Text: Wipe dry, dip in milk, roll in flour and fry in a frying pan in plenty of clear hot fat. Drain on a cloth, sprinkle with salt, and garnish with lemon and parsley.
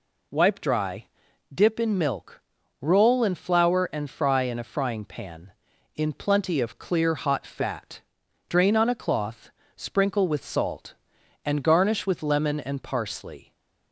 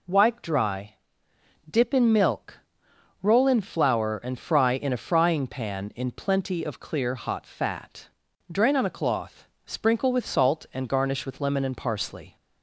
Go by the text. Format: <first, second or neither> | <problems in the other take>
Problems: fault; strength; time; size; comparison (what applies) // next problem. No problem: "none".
neither | none